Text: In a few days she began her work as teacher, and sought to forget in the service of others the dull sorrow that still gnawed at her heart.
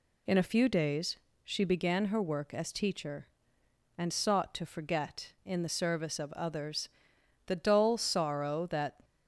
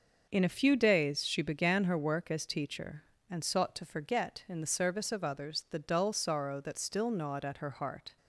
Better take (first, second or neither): second